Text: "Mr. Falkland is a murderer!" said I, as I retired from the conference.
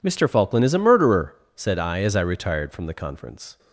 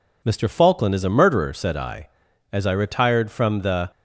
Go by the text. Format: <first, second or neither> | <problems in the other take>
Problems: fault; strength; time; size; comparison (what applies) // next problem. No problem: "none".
first | stops before "conference"; at 3.9 s